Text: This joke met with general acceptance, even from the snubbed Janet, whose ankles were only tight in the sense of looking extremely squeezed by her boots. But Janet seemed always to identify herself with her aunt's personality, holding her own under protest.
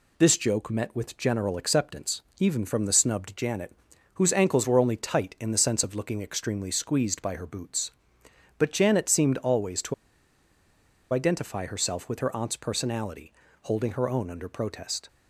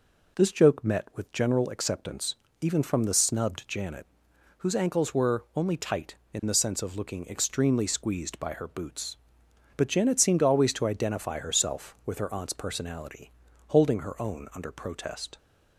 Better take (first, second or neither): second